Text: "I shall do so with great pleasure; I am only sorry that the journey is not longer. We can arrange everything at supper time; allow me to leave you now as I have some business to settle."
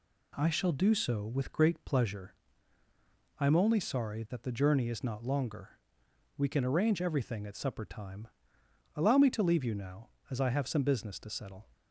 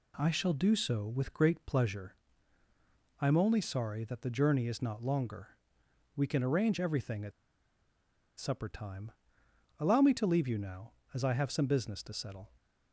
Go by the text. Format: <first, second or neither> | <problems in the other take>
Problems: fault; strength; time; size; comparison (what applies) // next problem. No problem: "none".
first | pauses between "at" and "supper"; at 7.3 s; 1.0 s long